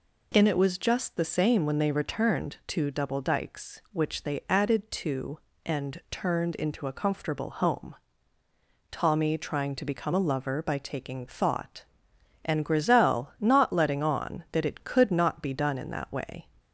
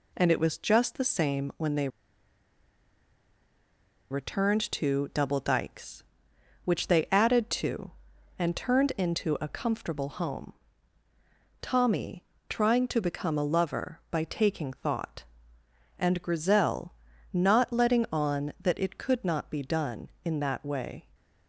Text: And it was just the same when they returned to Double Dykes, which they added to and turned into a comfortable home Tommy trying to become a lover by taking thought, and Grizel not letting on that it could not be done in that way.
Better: first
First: pauses between "home" and "Tommy"; noticeable; at 7.9 s; 0.96 s long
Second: pauses between "they" and "returned"; strong; at 1.8 s; 2.2 s long // pauses between "home" and "Tommy"; at 10.5 s; 1.0 s long // pauses between "Tommy" and "trying"; slight; at 12.2 s; 0.26 s long // pauses between "Grizel" and "not"; at 16.9 s; 0.38 s long

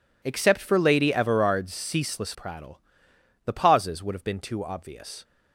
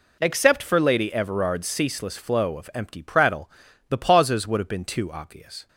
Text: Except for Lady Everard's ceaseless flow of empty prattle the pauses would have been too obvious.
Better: second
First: skips "flow of empty"; at 2.3 s // pauses between "prattle" and "the"; noticeable; at 2.7 s; 0.66 s long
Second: pauses between "prattle" and "the"; at 3.4 s; 0.40 s long

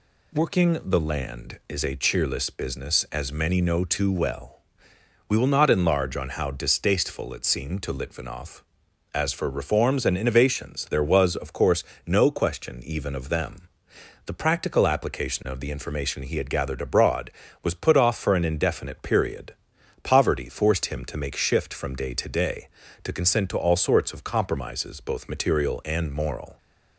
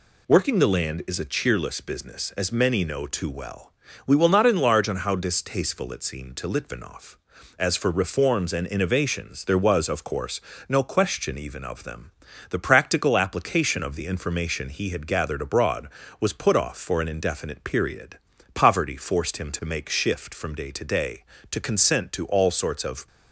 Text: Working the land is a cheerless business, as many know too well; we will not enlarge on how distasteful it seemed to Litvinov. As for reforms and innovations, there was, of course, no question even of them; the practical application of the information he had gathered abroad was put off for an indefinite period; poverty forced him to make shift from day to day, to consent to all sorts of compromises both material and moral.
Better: first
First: none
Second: stops before "compromises both material and moral"; at 23.0 s

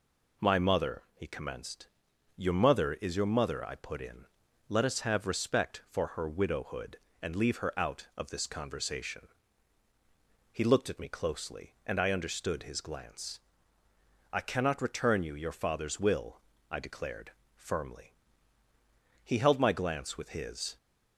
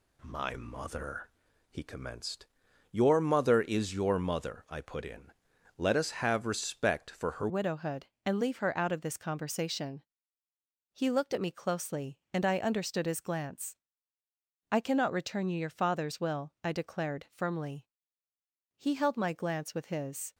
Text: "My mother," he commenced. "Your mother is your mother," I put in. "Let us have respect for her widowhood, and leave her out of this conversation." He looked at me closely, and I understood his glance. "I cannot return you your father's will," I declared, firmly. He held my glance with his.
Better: first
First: none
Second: changes voice at "widowhood"; from 7.4 s on; 12.9 s long

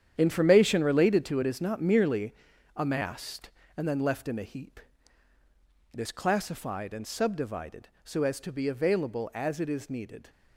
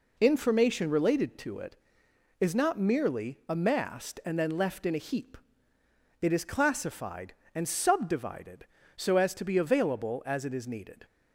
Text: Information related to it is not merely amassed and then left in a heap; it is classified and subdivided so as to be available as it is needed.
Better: second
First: gets quieter; strong; throughout; 11.5 dB // pauses between "merely" and "amassed"; at 2.3 s; 0.42 s long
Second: none

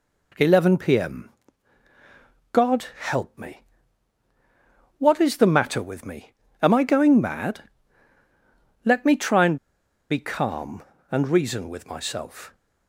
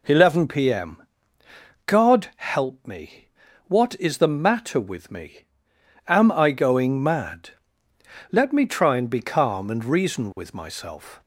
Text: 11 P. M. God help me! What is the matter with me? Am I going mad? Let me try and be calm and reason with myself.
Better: second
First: pauses between "M" and "God"; at 1.2 s; 1.2 s long // pauses between "and" and "be"; noticeable; at 9.5 s; 0.52 s long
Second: pauses between "M" and "God"; noticeable; at 1.0 s; 0.86 s long

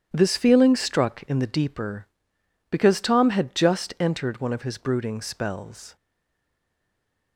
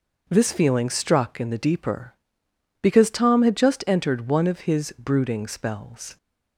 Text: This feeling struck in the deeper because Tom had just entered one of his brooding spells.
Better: second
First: starts louder than the rest; strong; until 1.1 s; 9.5 dB // stays silent after the last word; noticeable; from 5.9 s on; 1.4 s long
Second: none

